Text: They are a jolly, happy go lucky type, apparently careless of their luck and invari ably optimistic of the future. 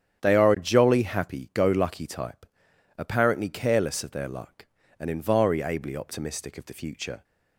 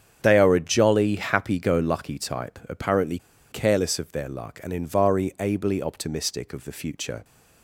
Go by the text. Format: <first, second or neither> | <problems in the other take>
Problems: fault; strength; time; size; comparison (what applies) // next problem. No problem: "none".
first | starts louder than the rest; strong; until 1.2 s; 8 dB; strong in the first // pauses between "apparently" and "careless"; slight; at 3.1 s; 0.32 s long